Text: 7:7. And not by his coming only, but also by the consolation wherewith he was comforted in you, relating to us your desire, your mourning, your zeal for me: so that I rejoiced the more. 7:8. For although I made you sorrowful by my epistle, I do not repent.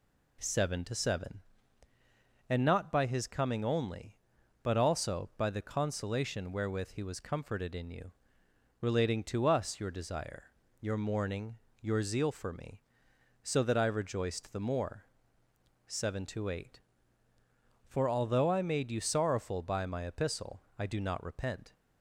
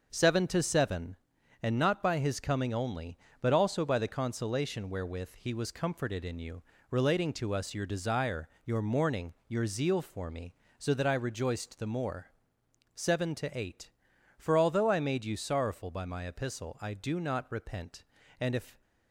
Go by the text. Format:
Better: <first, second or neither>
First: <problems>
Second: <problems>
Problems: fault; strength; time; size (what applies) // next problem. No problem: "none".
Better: first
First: none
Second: starts louder than the rest; noticeable; until 1.1 s; 6 dB // goes on to say "And if"; slight; from 18.4 s on; 0.40 s long